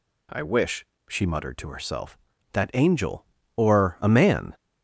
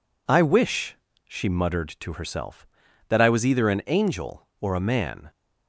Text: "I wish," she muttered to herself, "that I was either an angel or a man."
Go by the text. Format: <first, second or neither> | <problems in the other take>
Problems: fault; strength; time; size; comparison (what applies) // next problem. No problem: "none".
second | skips "I was either an"; at 2.7 s